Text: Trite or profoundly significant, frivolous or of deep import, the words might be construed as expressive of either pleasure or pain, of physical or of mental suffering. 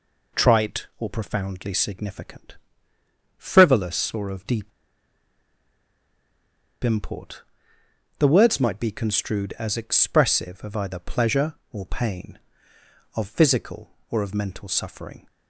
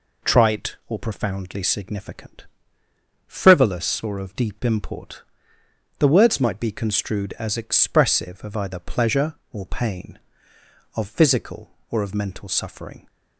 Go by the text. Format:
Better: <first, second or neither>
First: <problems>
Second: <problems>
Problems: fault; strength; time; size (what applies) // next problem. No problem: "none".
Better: second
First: pauses between "deep" and "import"; strong; at 4.7 s; 2.1 s long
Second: none